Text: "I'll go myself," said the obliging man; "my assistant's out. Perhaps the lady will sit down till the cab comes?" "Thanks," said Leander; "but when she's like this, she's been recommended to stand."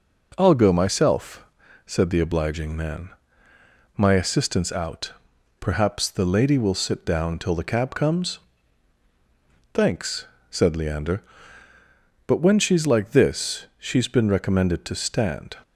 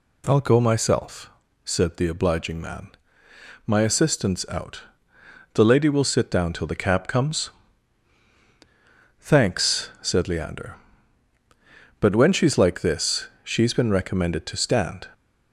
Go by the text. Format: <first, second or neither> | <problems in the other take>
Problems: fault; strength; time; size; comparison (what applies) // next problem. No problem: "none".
first | skips "Perhaps"; at 5.1 s